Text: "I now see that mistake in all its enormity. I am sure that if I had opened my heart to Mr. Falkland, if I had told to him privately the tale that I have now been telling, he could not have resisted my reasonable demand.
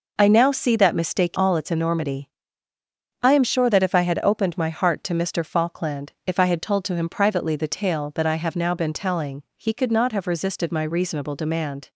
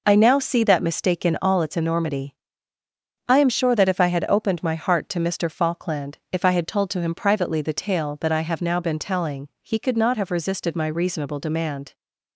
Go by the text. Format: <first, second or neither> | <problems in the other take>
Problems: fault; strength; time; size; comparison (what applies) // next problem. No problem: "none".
second | skips "in"; at 1.3 s